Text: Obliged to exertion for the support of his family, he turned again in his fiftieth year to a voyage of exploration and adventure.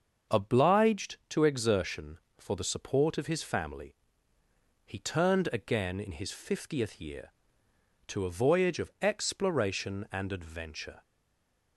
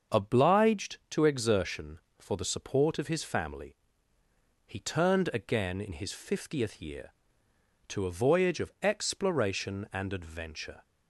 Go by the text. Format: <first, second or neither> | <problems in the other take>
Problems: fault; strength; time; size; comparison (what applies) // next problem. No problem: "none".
second | starts louder than the rest; until 1.4 s; 6.5 dB; also in the second // stays silent after the last word; slight; from 11.0 s on; 0.7 s long